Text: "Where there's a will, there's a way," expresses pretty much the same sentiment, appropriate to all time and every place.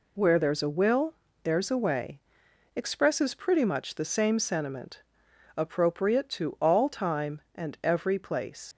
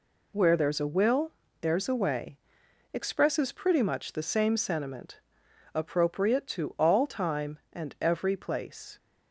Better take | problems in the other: second | leaves "place" unfinished; at 8.7 s; 90 ms

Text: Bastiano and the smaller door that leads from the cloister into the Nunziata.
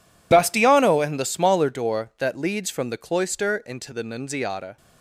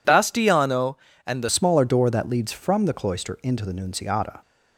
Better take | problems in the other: first | changes voice at "smaller"; from 1.4 s on; 3.0 s long

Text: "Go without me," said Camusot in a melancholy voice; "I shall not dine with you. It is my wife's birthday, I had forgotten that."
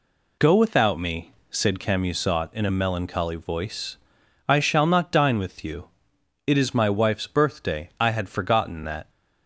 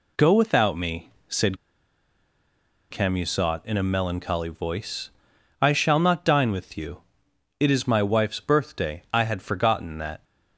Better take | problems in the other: first | pauses between "said" and "Camusot"; strong; at 1.5 s; 1.3 s long

